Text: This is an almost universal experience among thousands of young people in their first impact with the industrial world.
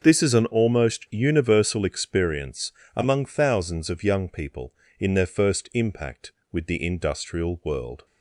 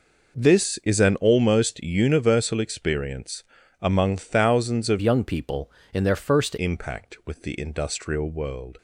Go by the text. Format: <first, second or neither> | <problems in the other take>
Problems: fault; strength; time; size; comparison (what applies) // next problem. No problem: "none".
first | pauses between "experience" and "among"; at 3.4 s; 0.38 s long; slight in the first // changes voice from "young" to "first"; from 5.0 to 6.5 s; 1.5 s long